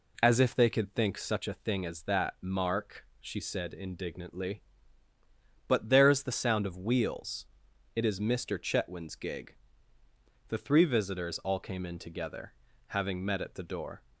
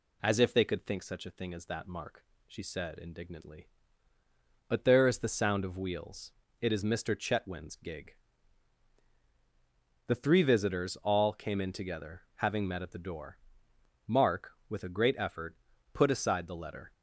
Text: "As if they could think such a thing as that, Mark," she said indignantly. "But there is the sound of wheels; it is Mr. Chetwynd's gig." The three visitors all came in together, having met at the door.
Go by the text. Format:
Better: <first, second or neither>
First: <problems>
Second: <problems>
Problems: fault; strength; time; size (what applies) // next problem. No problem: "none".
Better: first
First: none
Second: goes on to say "Mark with a great effort put aside the letter"; strong; from 14.0 s on; 2.8 s long